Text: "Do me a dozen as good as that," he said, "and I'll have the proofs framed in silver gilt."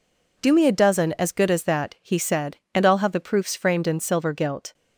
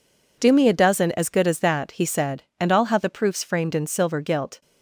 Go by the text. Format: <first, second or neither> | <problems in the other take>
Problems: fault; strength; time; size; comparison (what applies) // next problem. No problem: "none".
neither | none